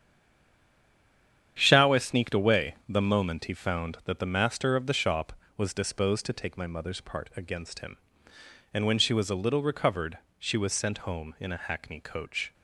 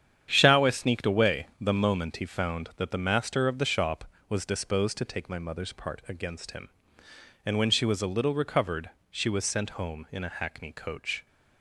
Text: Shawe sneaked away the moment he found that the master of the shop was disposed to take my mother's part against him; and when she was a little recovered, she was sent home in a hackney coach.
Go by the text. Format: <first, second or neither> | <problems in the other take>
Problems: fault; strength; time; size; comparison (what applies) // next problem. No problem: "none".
second | stays silent before the first word; noticeable; until 1.5 s; 1.5 s long // starts louder than the rest; strong; until 2.5 s; 9 dB; strong in the second